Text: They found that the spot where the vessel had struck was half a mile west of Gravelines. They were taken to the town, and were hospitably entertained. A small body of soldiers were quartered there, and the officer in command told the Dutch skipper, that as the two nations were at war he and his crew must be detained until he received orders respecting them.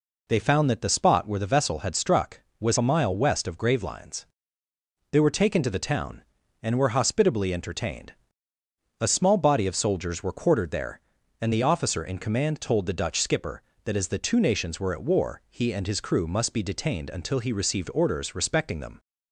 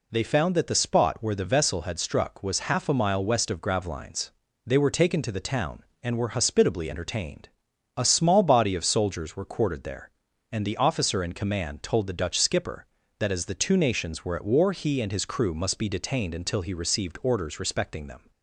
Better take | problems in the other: second | skips "half"; at 2.7 s

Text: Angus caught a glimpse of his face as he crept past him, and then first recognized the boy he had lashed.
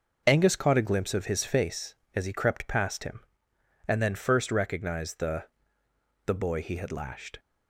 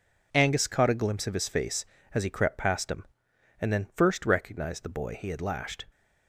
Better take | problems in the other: second | starts louder than the rest; noticeable; until 1.2 s; 6 dB // says "the" twice; at 6.2 s

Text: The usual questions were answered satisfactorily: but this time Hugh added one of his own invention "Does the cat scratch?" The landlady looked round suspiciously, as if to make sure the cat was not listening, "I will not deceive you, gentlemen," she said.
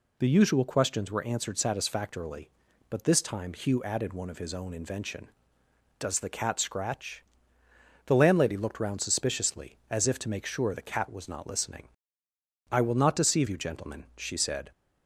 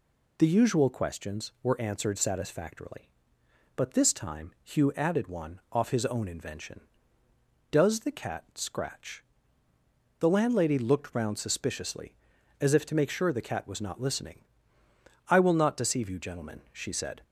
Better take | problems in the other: first | says "off" for "of"; at 5.7 s

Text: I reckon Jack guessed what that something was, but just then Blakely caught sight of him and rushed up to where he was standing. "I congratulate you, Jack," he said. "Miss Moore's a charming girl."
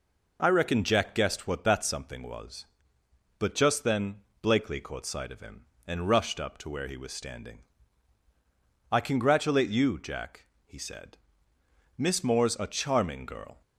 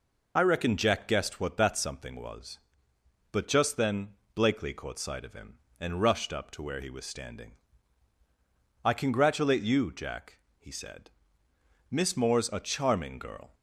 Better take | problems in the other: first | loses the start of "I"; at 0.3 s; 25 ms // pauses between "then" and "Blakely"; slight; at 4.0 s; 0.26 s long; slight in the first

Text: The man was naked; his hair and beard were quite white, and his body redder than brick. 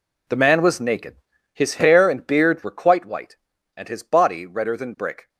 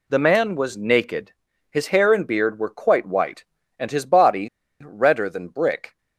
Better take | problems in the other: first | pauses between "body" and "redder"; at 4.4 s; 0.36 s long

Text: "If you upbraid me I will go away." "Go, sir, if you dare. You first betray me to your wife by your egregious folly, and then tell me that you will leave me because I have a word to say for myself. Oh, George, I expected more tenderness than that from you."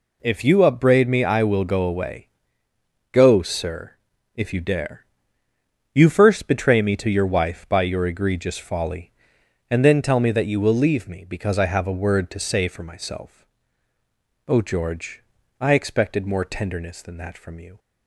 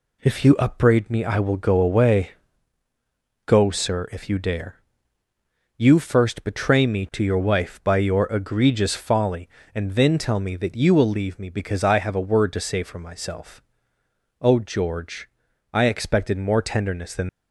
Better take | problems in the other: first | stops before "that from you"; at 17.2 s

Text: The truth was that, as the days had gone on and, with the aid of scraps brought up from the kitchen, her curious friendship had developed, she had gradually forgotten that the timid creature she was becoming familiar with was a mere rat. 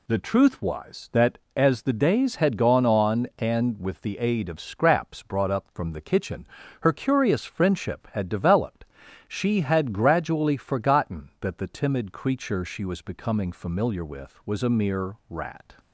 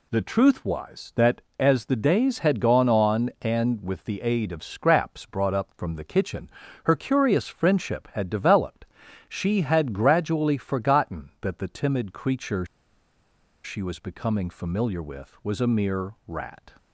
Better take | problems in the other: first | pauses between "creature" and "she"; at 12.6 s; 0.99 s long

